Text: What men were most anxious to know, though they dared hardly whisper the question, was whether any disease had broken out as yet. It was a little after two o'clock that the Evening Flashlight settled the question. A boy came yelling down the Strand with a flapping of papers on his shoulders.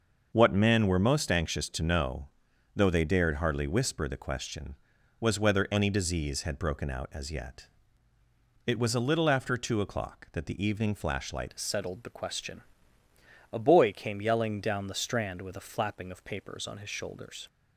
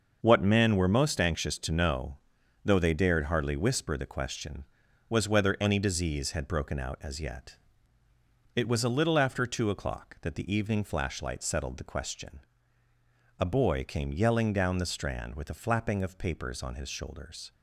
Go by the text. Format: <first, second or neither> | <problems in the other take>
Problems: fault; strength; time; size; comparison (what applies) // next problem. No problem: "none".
second | starts louder than the rest; until 1.3 s; 6.5 dB; also in the second // changes voice at "settled"; from 11.5 s on; 5.9 s long